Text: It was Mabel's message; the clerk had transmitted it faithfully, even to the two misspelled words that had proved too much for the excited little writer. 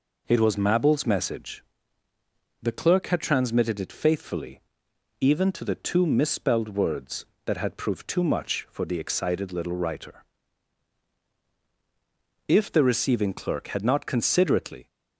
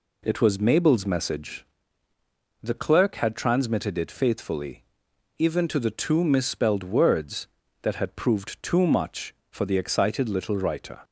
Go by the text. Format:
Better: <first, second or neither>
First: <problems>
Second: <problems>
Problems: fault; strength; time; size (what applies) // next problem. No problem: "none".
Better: second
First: goes on to say "If the receiving clerk had not considerately"; strong; from 12.4 s on; 2.3 s long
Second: none